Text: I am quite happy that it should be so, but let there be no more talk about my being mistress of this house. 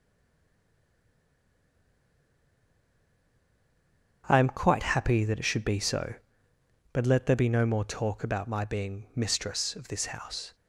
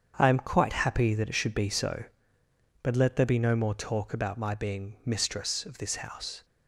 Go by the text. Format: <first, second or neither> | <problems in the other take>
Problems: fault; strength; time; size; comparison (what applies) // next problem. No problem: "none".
second | stays silent before the first word; strong; until 4.2 s; 4.2 s long // starts louder than the rest; strong; until 5.2 s; 7.5 dB; strong in the second